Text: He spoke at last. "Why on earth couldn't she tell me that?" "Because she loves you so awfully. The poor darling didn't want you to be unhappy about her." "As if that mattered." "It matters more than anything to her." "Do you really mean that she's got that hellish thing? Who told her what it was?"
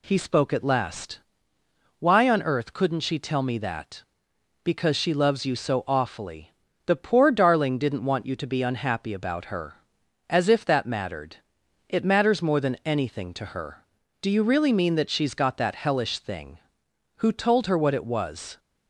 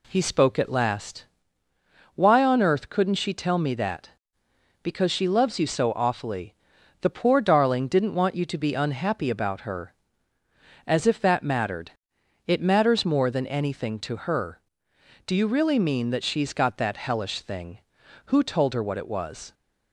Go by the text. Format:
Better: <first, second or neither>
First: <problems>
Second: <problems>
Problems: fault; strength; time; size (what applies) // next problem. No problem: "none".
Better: neither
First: none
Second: none